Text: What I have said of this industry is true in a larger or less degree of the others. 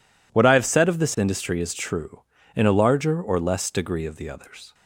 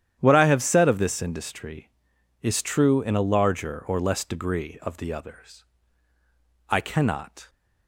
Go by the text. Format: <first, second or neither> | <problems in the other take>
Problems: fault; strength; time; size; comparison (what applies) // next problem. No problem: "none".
first | starts louder than the rest; strong; until 1.2 s; 10 dB // goes on to say "I cannot"; noticeable; from 6.6 s on; 0.80 s long